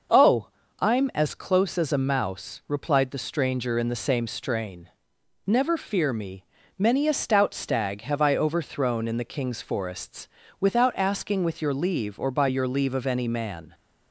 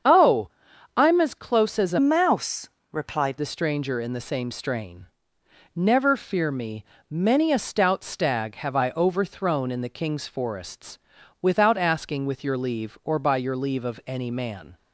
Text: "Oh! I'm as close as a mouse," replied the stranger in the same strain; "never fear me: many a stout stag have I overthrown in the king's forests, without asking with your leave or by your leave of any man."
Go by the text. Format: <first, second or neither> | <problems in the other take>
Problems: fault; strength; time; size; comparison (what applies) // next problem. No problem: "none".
first | starts louder than the rest; strong; until 1.5 s; 7.5 dB // changes voice from "mouse" to "replied"; from 1.9 to 3.3 s; 1.4 s long